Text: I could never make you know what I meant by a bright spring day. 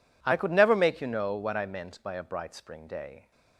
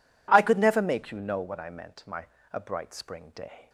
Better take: first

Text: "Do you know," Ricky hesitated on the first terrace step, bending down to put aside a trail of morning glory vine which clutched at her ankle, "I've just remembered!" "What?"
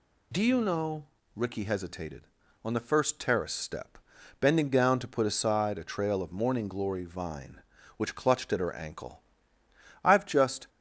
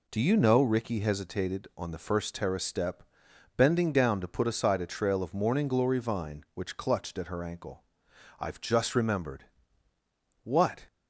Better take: second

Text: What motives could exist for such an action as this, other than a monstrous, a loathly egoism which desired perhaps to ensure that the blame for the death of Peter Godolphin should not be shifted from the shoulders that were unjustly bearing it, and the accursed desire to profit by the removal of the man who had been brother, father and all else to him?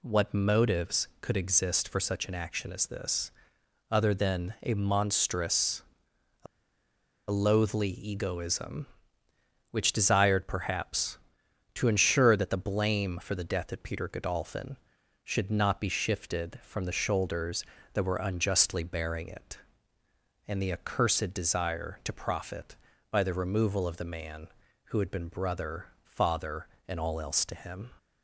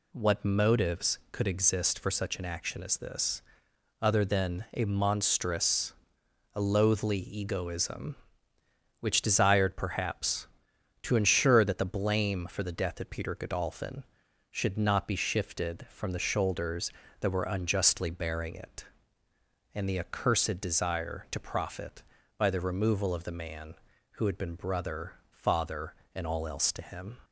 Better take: second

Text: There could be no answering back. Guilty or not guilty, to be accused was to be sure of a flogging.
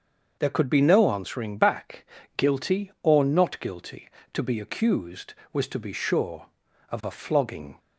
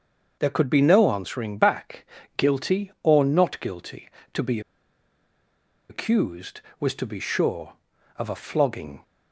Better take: first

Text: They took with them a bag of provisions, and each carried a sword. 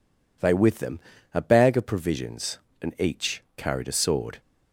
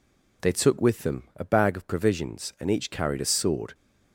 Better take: second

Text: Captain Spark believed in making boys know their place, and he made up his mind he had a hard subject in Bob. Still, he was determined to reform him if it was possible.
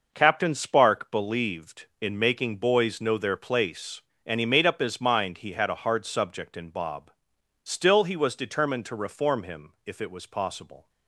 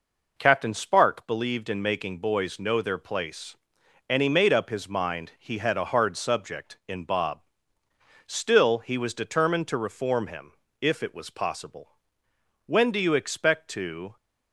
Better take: first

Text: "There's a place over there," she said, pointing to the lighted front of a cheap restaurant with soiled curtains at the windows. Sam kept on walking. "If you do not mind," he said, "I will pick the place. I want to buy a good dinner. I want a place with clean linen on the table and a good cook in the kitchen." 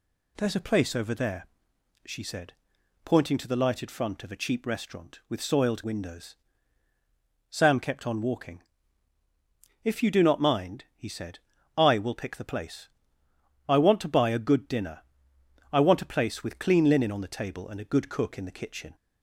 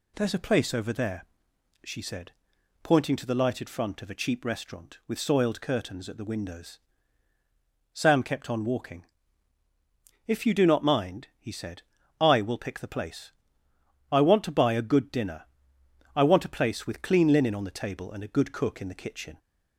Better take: second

